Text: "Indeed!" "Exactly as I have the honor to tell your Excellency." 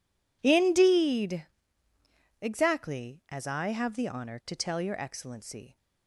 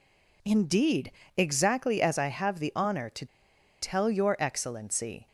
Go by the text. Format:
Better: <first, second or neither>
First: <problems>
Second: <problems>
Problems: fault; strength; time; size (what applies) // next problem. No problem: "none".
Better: first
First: none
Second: pauses between "to" and "tell"; noticeable; at 3.2 s; 0.54 s long